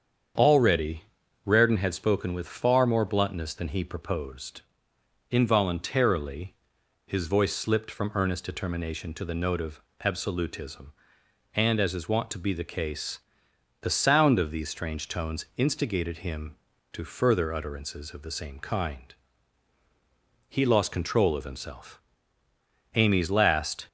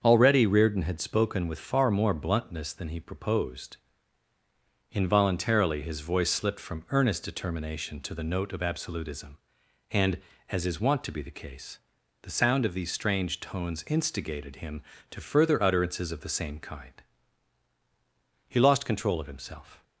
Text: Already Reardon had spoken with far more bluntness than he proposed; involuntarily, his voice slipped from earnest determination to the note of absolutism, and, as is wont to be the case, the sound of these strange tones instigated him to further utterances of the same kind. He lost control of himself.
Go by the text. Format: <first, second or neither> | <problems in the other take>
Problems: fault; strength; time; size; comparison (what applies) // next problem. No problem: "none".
second | starts louder than the rest; strong; until 1.7 s; 7.5 dB; also in the second // pauses between "Already" and "Reardon"; at 1.0 s; 0.42 s long // pauses between "of" and "absolutism"; slight; at 9.8 s; 0.24 s long // goes on to say "Amy's last"; noticeable; from 22.9 s on; 0.92 s long